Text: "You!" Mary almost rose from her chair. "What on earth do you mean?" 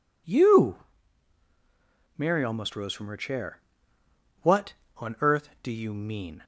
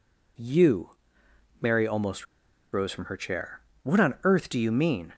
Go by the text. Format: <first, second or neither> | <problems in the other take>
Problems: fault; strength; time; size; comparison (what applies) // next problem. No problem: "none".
first | pauses between "almost" and "rose"; noticeable; at 2.2 s; 0.47 s long